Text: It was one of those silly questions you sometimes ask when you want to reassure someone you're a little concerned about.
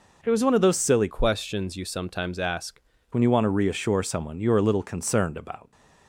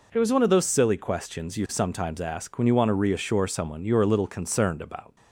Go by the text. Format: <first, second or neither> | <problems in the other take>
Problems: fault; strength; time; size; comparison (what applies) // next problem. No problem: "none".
second | changes voice from "questions" to "ask"; from 1.0 to 2.7 s; 1.7 s long